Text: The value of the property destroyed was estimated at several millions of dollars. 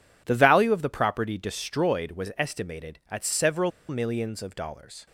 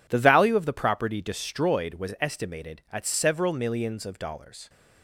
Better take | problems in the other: second | pauses between "several" and "millions"; slight; at 3.7 s; 0.19 s long

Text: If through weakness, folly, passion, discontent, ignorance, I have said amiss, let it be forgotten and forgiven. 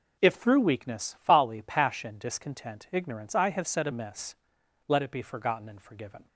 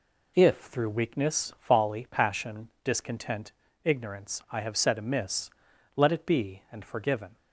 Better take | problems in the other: first | skips "forgotten"; at 6.6 s

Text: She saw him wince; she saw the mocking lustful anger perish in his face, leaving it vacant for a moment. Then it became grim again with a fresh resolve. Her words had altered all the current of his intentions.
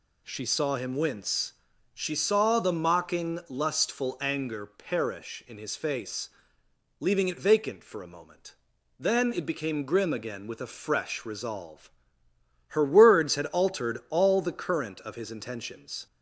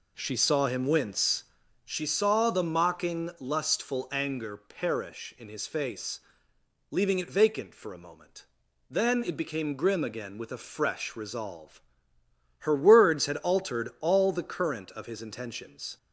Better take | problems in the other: first | starts louder than the rest; slight; until 1.9 s; 3.5 dB

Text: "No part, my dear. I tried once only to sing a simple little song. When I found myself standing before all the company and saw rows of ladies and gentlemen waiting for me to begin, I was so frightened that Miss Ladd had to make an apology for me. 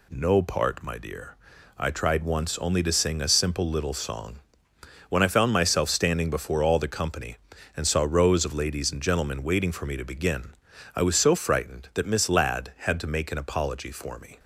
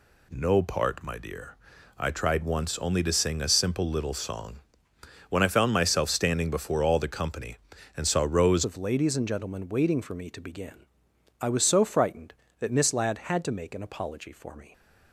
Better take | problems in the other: first | changes voice at "of"; from 8.6 s on; 6.1 s long

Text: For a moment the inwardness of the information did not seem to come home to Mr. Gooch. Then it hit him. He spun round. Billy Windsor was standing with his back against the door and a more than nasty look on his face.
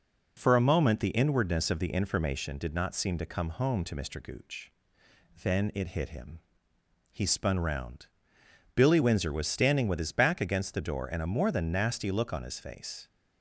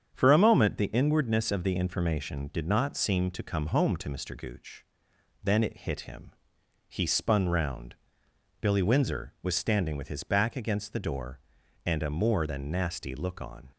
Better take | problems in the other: first | starts louder than the rest; strong; until 1.1 s; 7.5 dB // stops before "his face"; at 13.7 s

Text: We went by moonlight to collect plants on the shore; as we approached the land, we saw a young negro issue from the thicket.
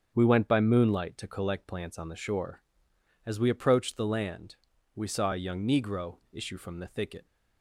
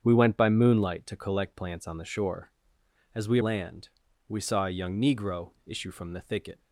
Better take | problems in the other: first | starts louder than the rest; strong; until 1.0 s; 8 dB; strong in the first // skips "approached the"; at 3.4 s

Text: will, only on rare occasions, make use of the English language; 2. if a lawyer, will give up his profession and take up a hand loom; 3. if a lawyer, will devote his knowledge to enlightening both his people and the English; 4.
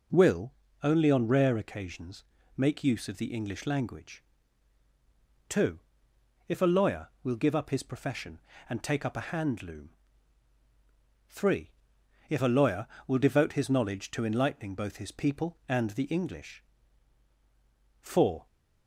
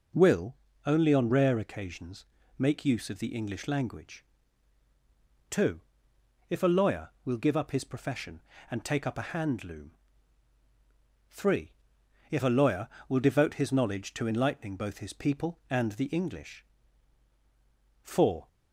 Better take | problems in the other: neither | none

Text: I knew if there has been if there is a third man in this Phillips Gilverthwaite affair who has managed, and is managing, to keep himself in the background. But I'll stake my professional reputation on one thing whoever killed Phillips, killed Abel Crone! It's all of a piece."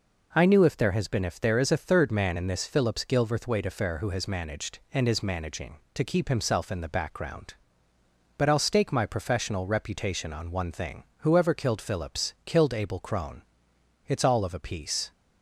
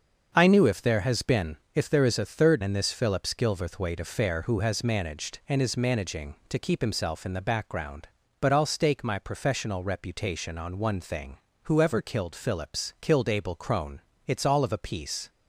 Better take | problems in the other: first | starts louder than the rest; until 1.3 s; 6.5 dB // pauses between "been" and "if"; slight; at 1.5 s; 0.18 s long // skips "man"; at 2.6 s // pauses between "thing" and "whoever"; slight; at 11.3 s; 0.24 s long; slight in the first

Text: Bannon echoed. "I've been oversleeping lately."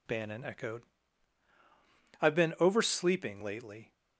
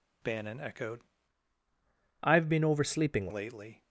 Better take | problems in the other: first | changes voice from "I've" to "oversleeping"; from 2.2 to 3.2 s; 1.0 s long

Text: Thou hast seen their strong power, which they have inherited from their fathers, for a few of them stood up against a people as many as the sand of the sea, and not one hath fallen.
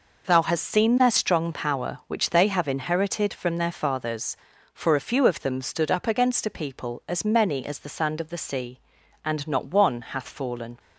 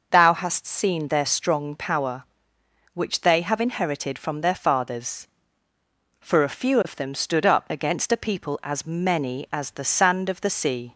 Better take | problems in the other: first | stops before "and not one hath fallen"; at 10.9 s

